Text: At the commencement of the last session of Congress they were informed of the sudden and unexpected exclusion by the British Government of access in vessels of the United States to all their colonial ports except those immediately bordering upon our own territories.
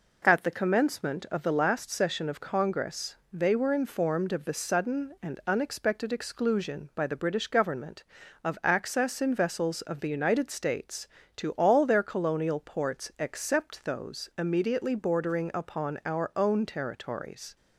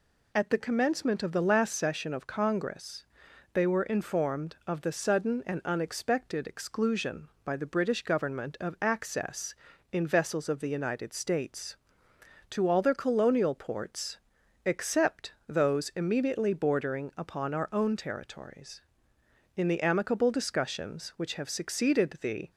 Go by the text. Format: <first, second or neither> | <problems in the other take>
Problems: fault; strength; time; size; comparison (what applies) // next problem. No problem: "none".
first | pauses between "Congress" and "they"; noticeable; at 3.0 s; 0.50 s long; slight in the first // pauses between "ports" and "except"; noticeable; at 14.1 s; 0.48 s long // goes on to say "In the amicable discussions which have succeeded the"; strong; from 19.5 s on; 2.9 s long